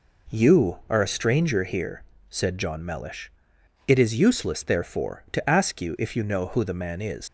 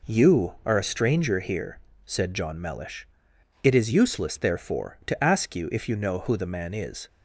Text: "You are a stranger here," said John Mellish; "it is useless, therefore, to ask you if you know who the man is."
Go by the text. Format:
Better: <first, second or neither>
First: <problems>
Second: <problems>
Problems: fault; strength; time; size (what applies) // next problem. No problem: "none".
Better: second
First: leaves "is" unfinished; at 7.2 s; 70 ms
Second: none